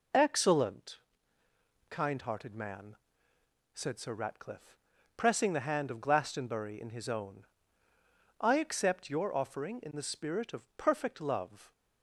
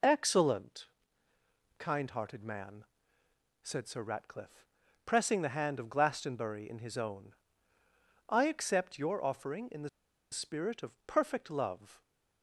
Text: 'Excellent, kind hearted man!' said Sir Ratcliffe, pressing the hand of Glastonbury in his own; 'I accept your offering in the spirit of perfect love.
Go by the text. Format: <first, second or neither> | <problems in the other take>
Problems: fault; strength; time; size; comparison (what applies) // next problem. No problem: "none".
first | pauses between "the" and "spirit"; at 9.8 s; 0.43 s long